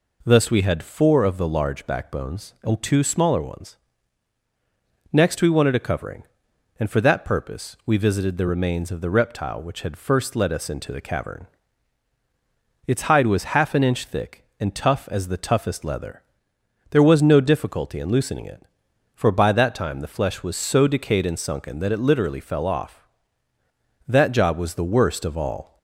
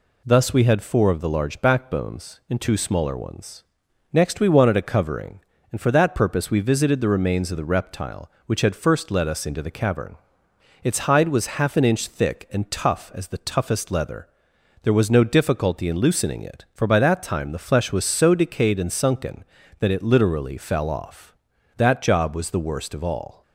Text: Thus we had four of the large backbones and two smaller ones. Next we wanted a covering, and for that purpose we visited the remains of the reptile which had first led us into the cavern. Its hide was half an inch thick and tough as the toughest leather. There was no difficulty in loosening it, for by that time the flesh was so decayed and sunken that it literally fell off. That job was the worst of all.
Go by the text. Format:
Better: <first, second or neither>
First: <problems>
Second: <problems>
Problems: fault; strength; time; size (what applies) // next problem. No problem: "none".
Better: neither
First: none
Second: none